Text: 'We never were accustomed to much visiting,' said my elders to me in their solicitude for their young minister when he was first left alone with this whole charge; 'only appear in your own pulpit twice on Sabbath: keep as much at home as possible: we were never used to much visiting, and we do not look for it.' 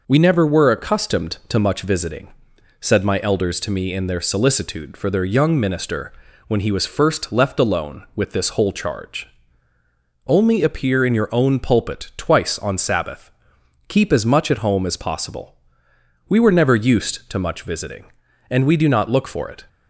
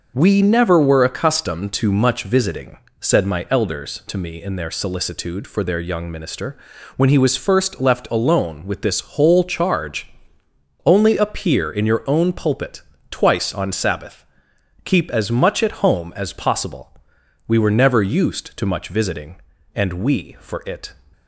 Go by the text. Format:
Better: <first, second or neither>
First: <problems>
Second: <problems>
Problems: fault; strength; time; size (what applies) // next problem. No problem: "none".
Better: first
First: pauses between "minister" and "when"; at 6.1 s; 0.38 s long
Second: pauses between "minister" and "when"; at 6.5 s; 0.38 s long // pauses between "pulpit" and "twice"; slight; at 12.8 s; 0.30 s long // skips "do not look"; at 20.3 s